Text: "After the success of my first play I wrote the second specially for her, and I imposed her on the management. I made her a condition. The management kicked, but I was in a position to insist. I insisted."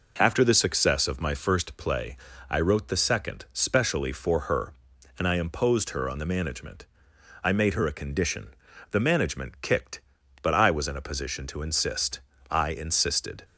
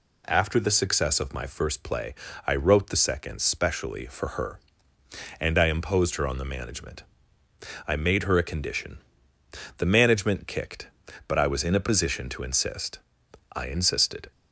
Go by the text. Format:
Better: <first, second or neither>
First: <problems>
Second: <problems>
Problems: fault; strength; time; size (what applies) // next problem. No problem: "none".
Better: neither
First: pauses between "play" and "I"; slight; at 2.1 s; 0.32 s long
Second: pauses between "play" and "I"; slight; at 2.1 s; 0.32 s long